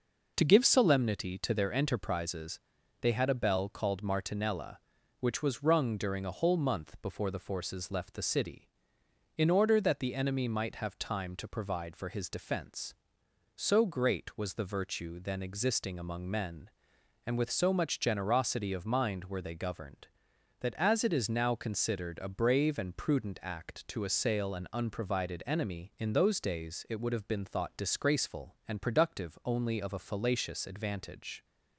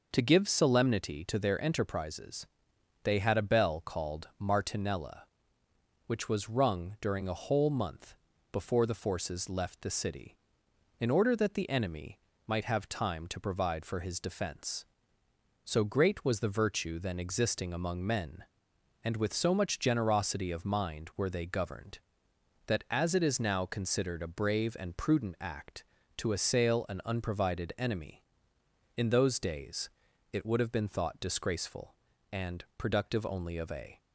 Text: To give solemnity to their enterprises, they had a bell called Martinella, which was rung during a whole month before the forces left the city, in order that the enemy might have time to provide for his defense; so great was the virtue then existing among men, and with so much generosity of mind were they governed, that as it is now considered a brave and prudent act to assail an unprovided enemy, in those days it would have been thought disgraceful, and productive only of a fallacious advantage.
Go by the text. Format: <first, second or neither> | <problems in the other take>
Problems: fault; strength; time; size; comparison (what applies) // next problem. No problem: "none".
first | pauses between "month" and "before"; slight; at 8.1 s; 0.36 s long // pauses between "enemy" and "might"; slight; at 12.1 s; 0.28 s long // pauses between "days" and "it"; at 29.9 s; 0.42 s long // stops before "fallacious advantage"; at 33.9 s